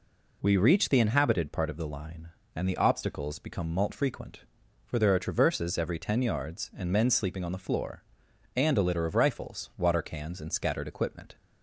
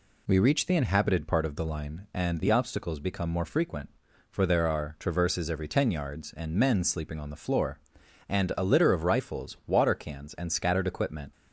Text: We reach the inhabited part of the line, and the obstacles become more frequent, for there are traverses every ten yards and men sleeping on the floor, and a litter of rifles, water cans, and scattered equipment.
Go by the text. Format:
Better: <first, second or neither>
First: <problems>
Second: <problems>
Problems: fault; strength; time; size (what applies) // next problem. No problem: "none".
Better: second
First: says "malt" for "more"; at 3.7 s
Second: none